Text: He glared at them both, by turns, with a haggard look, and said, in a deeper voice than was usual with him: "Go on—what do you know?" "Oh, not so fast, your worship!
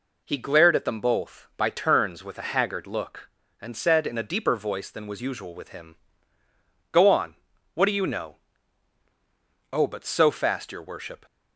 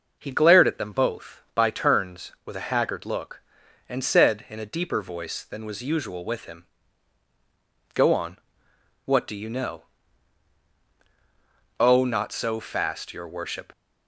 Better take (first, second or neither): second